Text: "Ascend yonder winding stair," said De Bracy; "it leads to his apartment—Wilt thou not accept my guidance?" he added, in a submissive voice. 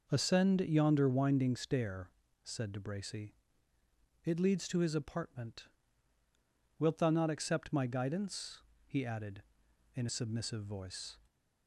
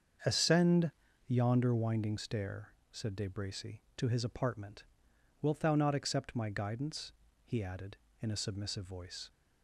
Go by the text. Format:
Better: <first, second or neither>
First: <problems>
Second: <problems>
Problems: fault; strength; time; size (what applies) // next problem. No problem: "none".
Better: first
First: none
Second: starts louder than the rest; until 1.6 s; 7 dB // pauses between "Ascend" and "yonder"; slight; at 0.9 s; 0.36 s long // skips "it leads"; at 3.8 s